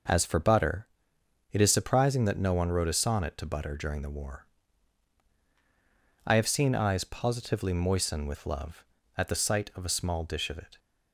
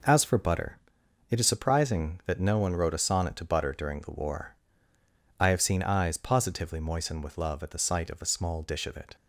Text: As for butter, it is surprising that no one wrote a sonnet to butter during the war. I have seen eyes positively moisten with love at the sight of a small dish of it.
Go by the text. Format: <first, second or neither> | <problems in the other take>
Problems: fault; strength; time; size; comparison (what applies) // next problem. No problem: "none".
neither | none